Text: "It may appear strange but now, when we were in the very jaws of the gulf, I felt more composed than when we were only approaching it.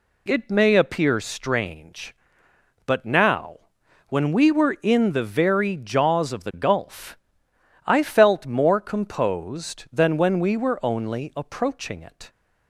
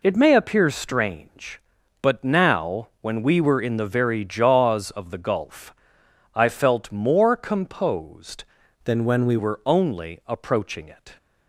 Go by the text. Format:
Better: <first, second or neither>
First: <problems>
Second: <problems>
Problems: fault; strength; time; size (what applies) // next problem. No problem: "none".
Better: first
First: none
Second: changes voice from "than" to "we"; from 8.8 to 9.3 s; 0.5 s long